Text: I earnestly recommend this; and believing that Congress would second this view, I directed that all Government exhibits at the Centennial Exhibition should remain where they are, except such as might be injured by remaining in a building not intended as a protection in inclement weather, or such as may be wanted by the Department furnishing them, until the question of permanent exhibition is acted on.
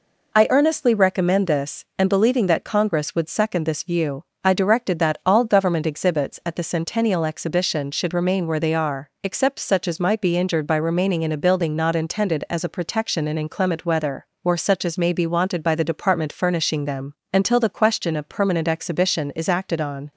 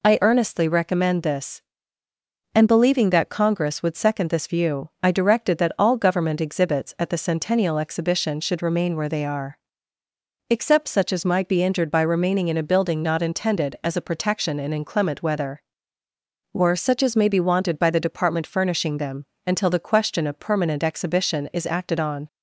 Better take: neither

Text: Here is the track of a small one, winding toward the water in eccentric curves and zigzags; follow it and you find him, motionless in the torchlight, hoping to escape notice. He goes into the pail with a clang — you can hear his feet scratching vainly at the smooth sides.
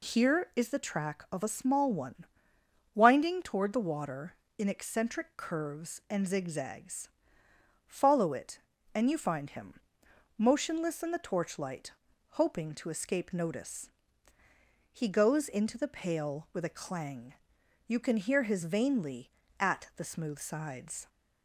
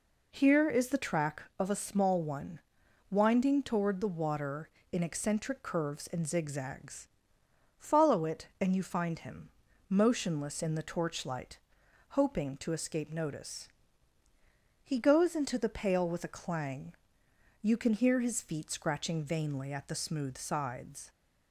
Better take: second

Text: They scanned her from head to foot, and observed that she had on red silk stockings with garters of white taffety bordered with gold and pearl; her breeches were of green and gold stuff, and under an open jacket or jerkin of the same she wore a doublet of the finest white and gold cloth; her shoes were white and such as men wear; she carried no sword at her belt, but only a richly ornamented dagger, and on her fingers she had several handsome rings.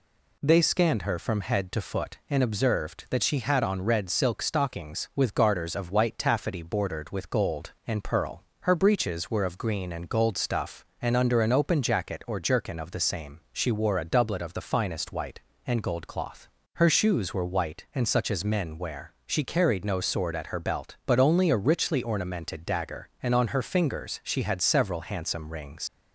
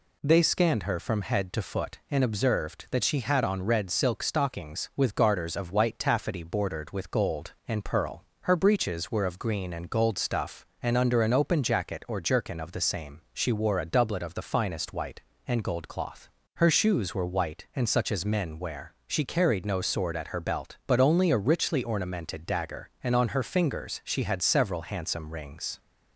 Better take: second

